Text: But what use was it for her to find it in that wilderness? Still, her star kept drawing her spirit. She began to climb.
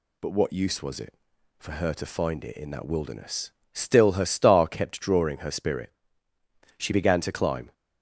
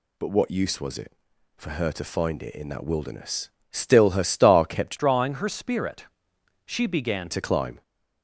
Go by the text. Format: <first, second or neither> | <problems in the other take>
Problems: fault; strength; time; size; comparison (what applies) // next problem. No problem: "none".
first | changes voice from "drawing" to "began"; from 4.9 to 7.2 s; 2.3 s long